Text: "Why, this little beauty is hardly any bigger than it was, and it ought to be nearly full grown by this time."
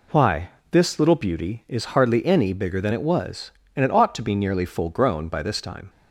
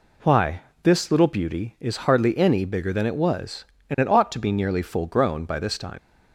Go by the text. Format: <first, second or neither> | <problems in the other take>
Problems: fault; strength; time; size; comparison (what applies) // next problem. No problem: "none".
first | leaves "time" unfinished; at 5.9 s; 75 ms